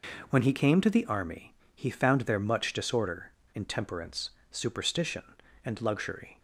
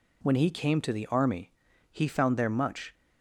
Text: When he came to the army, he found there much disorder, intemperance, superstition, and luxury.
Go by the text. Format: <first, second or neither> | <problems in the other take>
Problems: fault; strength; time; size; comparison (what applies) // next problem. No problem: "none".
first | stops before "disorder intemperance superstition and luxury"; at 2.9 s